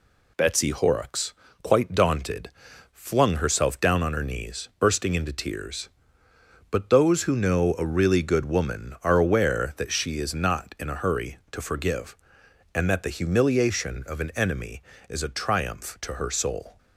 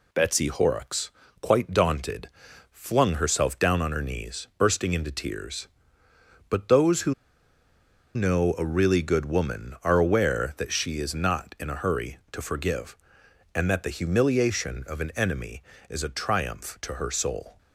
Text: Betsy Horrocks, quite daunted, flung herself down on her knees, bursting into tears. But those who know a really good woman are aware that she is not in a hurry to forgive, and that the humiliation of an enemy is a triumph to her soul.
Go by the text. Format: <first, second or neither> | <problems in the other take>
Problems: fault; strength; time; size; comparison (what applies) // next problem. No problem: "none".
first | pauses between "who" and "know"; at 7.1 s; 1.0 s long